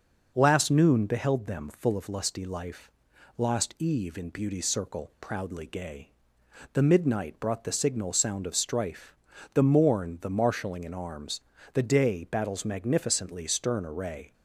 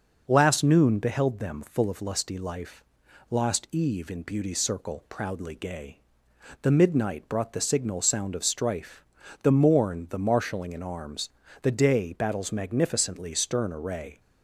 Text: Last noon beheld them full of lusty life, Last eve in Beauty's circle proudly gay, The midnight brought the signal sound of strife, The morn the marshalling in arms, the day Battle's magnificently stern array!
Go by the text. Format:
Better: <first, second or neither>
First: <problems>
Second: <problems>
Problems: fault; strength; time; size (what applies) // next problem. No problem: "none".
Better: neither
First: none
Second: none